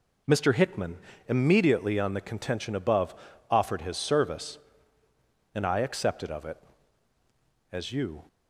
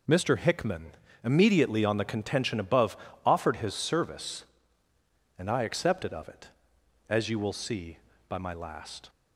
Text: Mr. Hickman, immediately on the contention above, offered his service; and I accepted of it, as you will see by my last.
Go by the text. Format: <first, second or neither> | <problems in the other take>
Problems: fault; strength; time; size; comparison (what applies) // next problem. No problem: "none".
second | stops before "will see by my last"; at 8.2 s